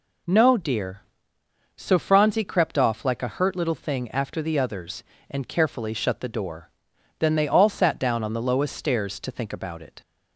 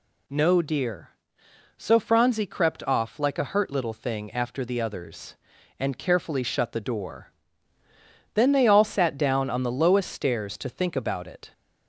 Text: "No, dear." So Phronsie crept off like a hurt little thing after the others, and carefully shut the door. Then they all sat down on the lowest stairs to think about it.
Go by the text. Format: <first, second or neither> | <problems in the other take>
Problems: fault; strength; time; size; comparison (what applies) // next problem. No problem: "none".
neither | none